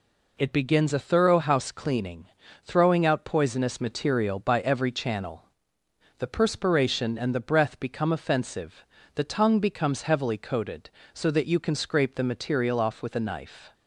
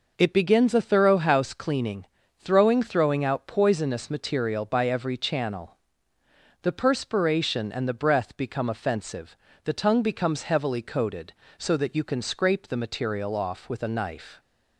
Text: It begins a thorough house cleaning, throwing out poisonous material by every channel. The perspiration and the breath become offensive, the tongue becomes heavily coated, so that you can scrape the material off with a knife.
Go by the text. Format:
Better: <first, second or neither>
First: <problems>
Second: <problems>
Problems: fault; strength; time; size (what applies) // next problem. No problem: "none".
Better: first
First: none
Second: says "throwing" twice; at 2.8 s